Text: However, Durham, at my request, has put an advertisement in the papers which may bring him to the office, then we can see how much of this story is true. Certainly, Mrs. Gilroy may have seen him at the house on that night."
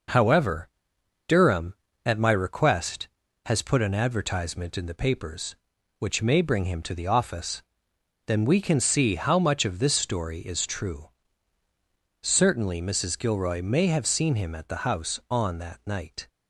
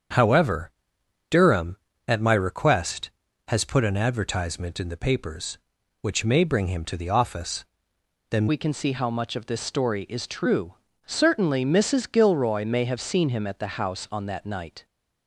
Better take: first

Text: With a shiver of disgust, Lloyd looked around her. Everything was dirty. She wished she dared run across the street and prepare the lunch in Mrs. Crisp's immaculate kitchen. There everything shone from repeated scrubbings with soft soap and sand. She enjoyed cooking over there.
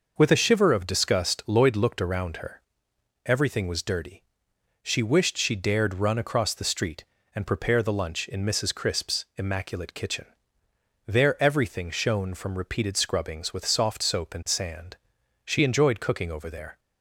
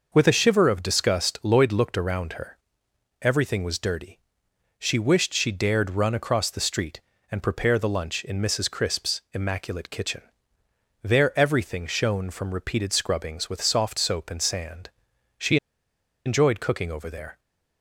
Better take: first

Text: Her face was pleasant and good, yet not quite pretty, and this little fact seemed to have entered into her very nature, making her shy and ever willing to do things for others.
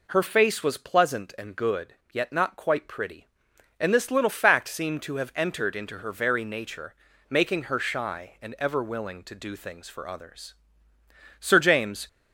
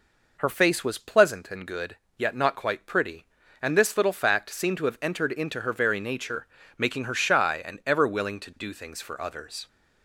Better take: second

